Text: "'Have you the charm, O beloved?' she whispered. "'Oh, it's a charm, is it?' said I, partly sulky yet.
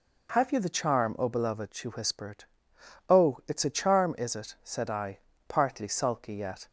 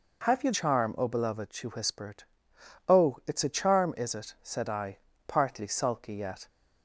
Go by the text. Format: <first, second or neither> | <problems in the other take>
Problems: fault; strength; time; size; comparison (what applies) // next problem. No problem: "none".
first | skips "the"; at 0.5 s